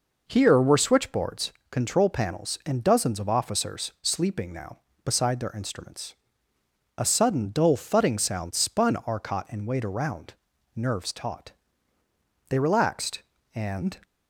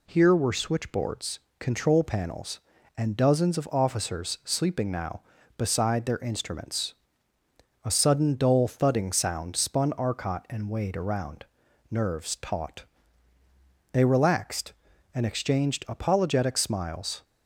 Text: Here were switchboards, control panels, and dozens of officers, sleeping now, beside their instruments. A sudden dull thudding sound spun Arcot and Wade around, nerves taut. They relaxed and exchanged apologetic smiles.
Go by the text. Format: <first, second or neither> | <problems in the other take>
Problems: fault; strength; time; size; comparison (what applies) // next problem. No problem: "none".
second | stops before "exchanged apologetic smiles"; at 14.0 s